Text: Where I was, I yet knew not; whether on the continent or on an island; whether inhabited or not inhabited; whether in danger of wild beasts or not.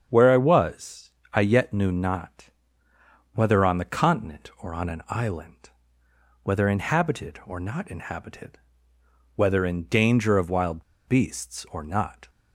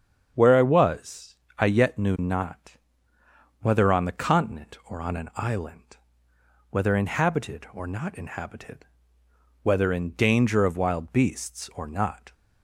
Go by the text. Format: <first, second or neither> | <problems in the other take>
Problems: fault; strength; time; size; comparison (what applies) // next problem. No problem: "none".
second | starts louder than the rest; strong; until 1.1 s; 7 dB; strong in the second // pauses between "wild" and "beasts"; slight; at 10.8 s; 0.25 s long